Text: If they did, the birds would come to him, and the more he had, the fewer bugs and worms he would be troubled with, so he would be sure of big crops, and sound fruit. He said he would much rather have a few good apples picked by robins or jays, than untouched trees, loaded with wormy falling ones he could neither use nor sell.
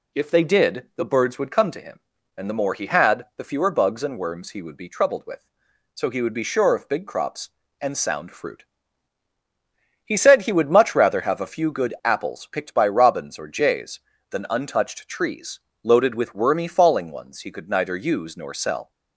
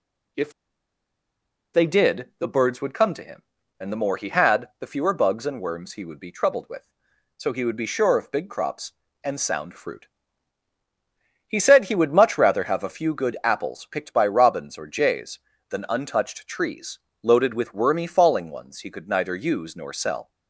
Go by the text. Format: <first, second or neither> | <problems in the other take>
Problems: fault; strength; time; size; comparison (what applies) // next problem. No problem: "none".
first | pauses between "If" and "they"; at 0.5 s; 1.2 s long